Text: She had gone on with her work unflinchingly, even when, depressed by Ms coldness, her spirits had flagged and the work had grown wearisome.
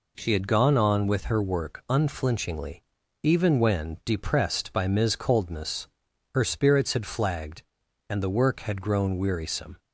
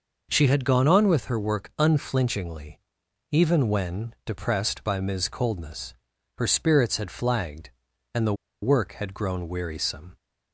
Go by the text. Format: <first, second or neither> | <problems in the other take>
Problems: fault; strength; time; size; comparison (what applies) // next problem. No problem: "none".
first | pauses between "the" and "work"; slight; at 8.3 s; 0.28 s long